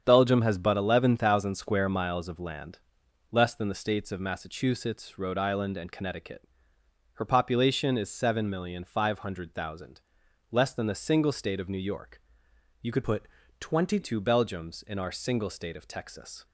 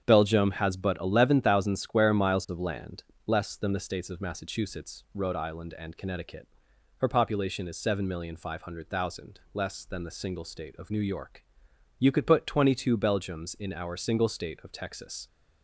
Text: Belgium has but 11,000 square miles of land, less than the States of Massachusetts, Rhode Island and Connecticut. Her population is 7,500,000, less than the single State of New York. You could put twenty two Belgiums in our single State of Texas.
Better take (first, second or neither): second